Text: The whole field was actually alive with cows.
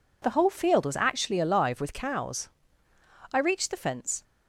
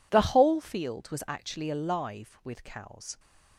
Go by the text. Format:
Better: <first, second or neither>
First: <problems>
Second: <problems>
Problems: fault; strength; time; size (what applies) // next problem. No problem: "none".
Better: second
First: goes on to say "I reached the fence"; noticeable; from 3.3 s on; 0.92 s long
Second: none